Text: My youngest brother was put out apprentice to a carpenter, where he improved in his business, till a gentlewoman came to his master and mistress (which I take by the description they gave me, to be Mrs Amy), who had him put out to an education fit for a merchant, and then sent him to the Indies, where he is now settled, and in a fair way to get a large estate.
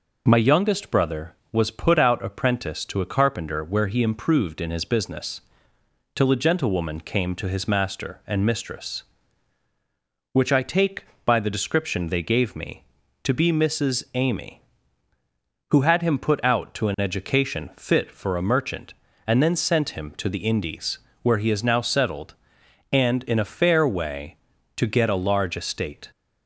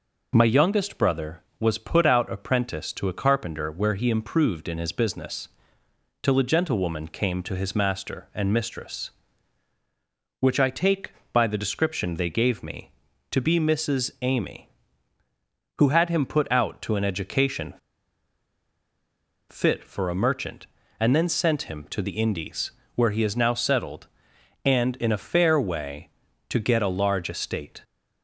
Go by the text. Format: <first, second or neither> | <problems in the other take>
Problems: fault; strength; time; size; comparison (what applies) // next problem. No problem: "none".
first | pauses between "education" and "fit"; strong; at 17.7 s; 1.7 s long